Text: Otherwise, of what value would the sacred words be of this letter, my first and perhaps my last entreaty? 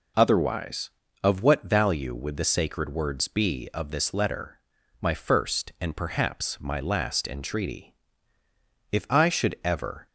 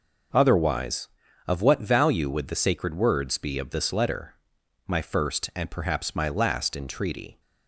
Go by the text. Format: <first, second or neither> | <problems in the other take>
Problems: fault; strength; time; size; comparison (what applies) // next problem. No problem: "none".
second | goes on to say "If I should ever"; noticeable; from 8.9 s on; 1.1 s long